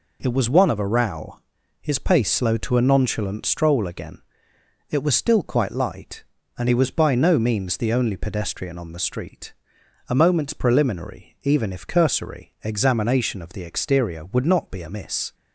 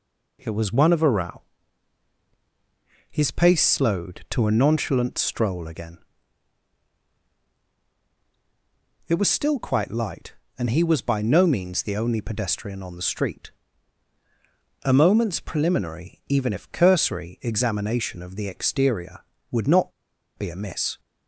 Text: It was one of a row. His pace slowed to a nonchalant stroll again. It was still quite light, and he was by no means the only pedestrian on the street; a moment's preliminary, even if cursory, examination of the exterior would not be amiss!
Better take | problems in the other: first | pauses between "not" and "be"; noticeable; at 19.9 s; 0.46 s long

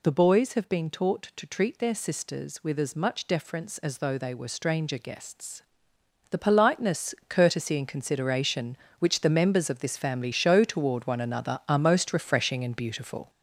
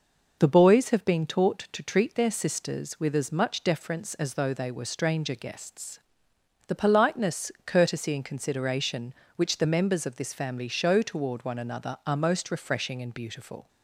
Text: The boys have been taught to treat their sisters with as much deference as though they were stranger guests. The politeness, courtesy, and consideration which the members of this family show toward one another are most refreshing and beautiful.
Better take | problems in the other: second | gets louder; noticeable; throughout; 5.5 dB

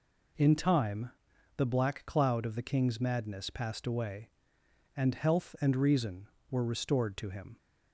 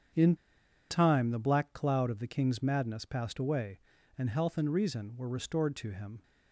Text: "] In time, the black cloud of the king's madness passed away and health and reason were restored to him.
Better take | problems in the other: first | starts louder than the rest; strong; until 1.6 s; 8 dB // pauses between "In" and "time"; noticeable; at 0.3 s; 0.55 s long

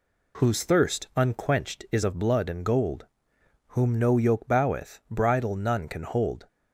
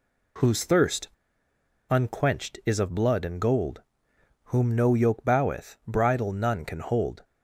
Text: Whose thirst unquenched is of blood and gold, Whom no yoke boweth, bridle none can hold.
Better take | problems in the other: first | pauses between "thirst" and "unquenched"; noticeable; at 1.0 s; 0.81 s long

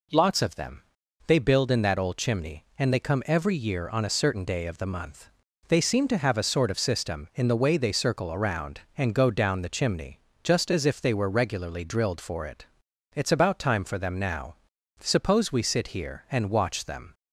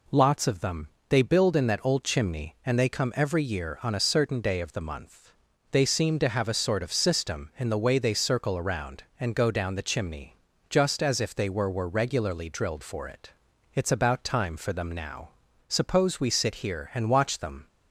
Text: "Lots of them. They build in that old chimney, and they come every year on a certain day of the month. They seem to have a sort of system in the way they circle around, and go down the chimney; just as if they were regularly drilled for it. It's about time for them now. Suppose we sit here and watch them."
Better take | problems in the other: first | says "were" twice; at 11.6 s

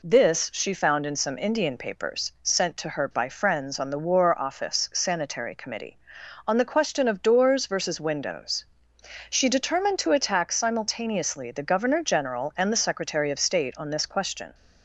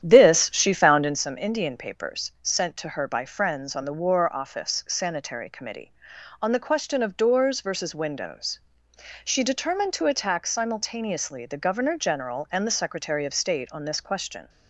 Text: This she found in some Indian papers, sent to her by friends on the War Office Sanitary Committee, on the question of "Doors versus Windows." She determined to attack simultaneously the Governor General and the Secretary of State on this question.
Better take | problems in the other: first | starts louder than the rest; strong; until 1.2 s; 10 dB

